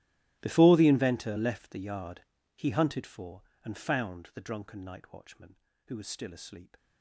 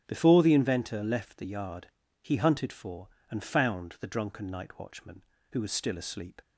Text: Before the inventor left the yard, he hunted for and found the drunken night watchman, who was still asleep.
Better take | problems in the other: second | gets quieter; strong; throughout; 21.5 dB // starts louder than the rest; strong; until 1.4 s; 17 dB; strong in the second

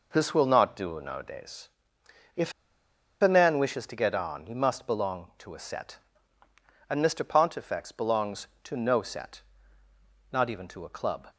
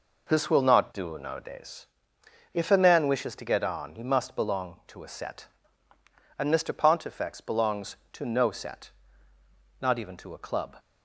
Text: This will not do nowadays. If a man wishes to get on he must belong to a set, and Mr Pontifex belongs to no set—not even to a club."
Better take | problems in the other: second | pauses between "If" and "a"; noticeable; at 2.5 s; 0.69 s long

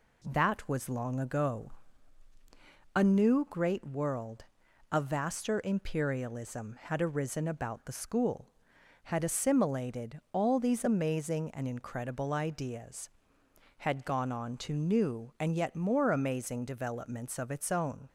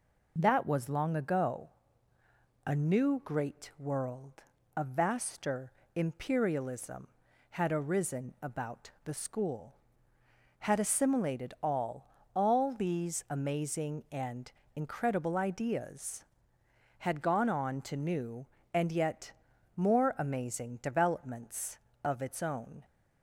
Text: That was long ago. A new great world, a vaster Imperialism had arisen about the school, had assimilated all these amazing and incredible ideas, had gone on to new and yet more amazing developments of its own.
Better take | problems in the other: first | pauses between "vaster" and "Imperialism"; slight; at 5.7 s; 0.24 s long // says "all" twice; at 12.3 s // pauses between "and" and "incredible"; slight; at 14.5 s; 0.24 s long // pauses between "yet" and "more"; at 19.3 s; 0.44 s long

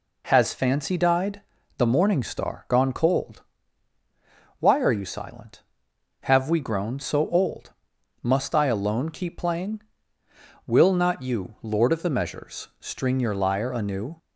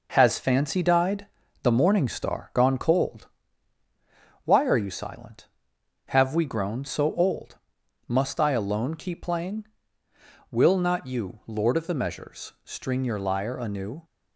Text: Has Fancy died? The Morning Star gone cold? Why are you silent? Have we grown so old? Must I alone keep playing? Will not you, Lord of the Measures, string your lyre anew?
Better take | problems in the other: first | gets quieter; noticeable; throughout; 4.5 dB

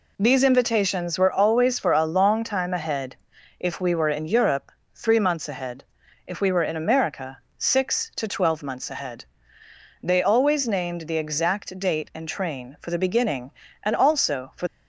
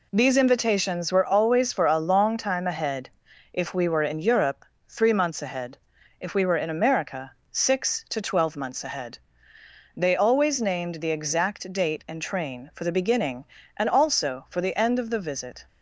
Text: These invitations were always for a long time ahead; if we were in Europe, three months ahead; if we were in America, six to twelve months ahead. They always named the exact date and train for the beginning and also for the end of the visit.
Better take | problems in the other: second | stops before "the end of the visit"; at 14.6 s

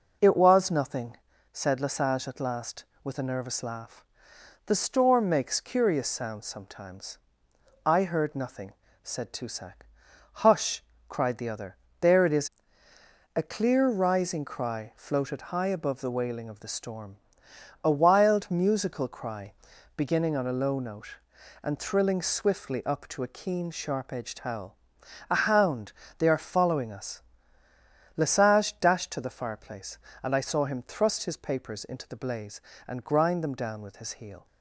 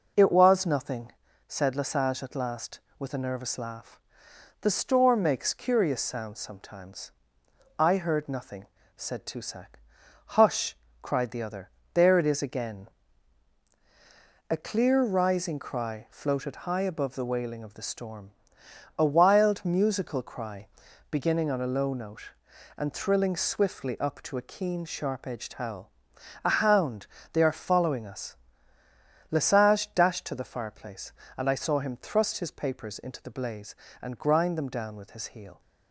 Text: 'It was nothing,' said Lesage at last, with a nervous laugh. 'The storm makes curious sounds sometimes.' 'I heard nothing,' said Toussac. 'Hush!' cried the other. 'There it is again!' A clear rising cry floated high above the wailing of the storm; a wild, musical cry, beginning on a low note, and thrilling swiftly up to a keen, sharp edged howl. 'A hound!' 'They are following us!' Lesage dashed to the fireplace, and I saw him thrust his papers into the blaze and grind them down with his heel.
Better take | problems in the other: second | skips "again"; at 12.9 s

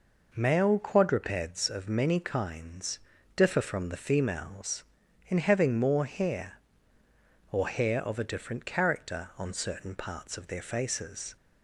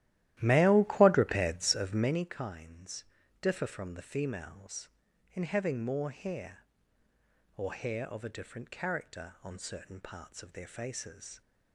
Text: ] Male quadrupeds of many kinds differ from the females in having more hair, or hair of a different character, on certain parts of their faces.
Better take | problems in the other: first | starts louder than the rest; strong; until 2.3 s; 14 dB // pauses between "kinds" and "differ"; slight; at 3.0 s; 0.36 s long; slight in the first

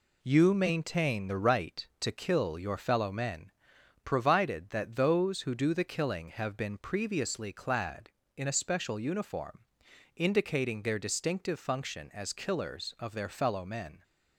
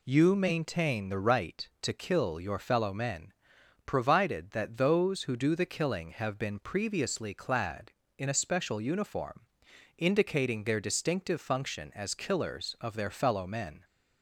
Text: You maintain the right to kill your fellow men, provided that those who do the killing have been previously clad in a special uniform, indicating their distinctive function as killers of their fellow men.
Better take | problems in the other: second | gets quieter; noticeable; throughout; 5.5 dB

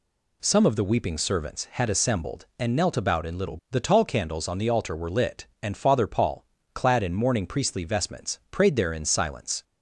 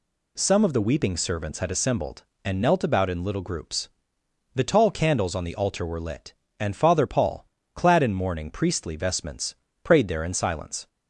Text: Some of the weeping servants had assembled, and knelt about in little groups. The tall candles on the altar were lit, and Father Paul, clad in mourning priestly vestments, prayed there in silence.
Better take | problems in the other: second | skips "groups"; at 3.6 s

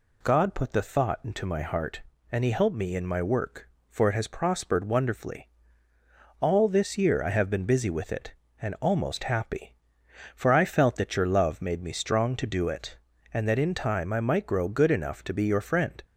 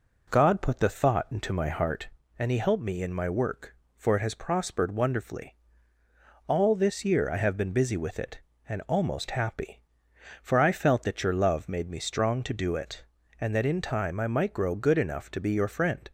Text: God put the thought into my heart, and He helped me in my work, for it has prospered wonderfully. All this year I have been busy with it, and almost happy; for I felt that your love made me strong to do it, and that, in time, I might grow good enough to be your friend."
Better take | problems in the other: first | starts louder than the rest; noticeable; until 2.2 s; 4.5 dB

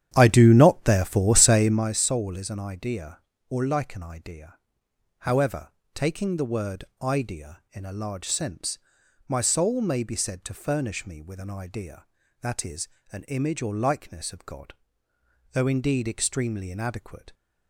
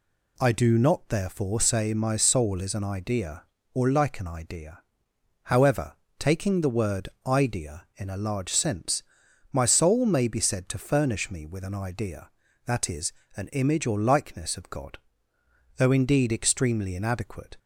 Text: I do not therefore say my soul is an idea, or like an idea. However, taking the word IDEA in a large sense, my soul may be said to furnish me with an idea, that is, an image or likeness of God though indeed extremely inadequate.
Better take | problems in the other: second | starts louder than the rest; strong; until 2.0 s; 10 dB // pauses between "word" and "IDEA"; slight; at 6.8 s; 0.16 s long; slight in the second // pauses between "God" and "though"; noticeable; at 14.7 s; 0.80 s long; noticeable in the second

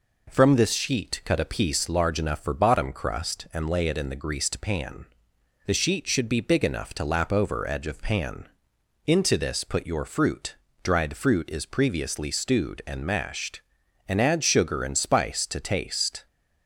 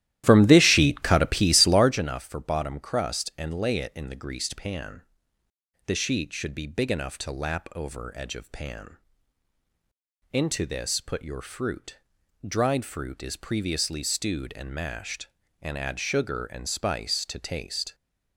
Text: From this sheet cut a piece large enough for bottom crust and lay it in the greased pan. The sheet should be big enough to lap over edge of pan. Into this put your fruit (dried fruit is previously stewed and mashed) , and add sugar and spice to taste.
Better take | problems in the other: first | starts louder than the rest; strong; until 2.0 s; 13.5 dB

